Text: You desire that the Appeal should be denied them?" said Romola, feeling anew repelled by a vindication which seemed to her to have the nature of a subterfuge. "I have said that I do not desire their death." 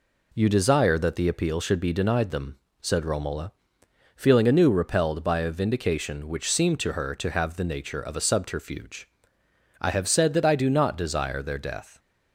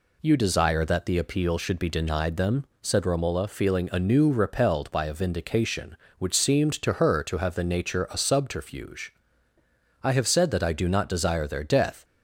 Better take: first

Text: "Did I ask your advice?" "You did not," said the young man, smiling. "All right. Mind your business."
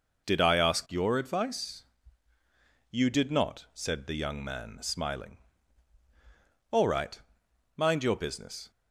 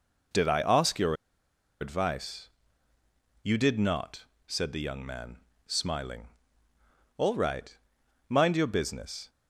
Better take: first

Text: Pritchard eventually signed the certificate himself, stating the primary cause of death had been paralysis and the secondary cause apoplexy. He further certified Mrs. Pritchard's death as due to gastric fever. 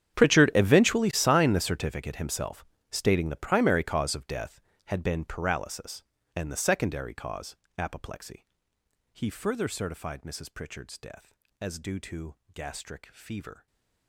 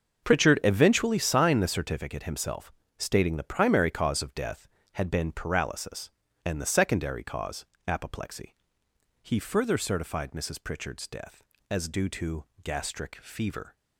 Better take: second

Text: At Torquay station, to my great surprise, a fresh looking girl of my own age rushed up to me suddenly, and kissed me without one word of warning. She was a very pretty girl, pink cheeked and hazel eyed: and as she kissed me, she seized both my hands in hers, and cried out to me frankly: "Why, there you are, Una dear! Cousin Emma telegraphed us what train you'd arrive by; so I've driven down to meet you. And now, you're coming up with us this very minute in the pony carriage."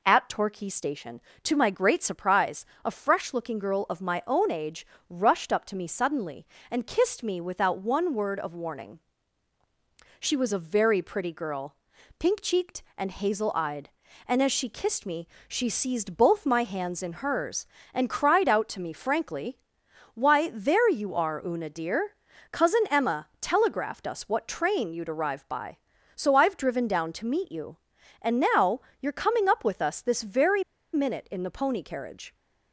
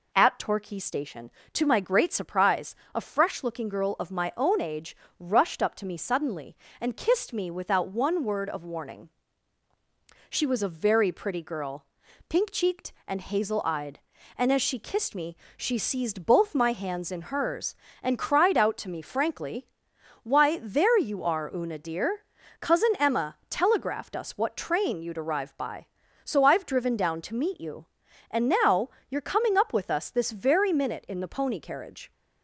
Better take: second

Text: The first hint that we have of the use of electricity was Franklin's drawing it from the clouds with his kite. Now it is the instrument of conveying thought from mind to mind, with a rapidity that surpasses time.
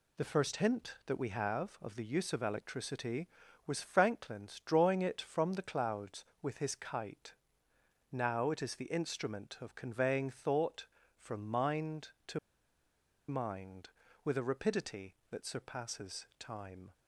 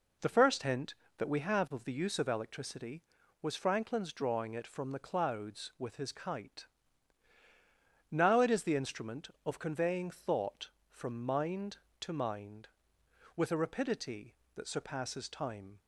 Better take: second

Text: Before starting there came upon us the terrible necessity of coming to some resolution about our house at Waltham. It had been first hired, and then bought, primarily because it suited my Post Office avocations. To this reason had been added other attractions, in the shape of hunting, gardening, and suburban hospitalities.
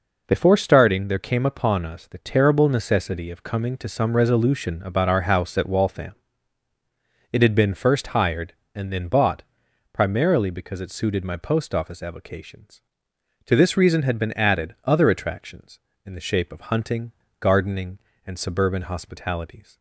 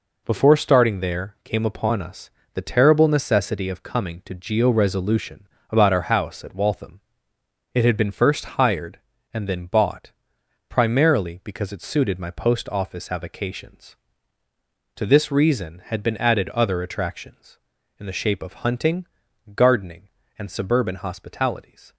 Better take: first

